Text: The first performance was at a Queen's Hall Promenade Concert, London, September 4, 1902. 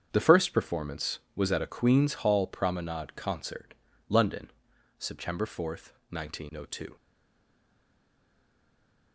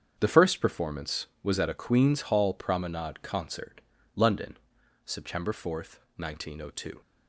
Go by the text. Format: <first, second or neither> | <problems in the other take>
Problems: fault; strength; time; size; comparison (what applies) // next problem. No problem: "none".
second | starts louder than the rest; strong; until 1.1 s; 7.5 dB; strong in the second // stays silent after the last word; from 6.9 s on; 2.2 s long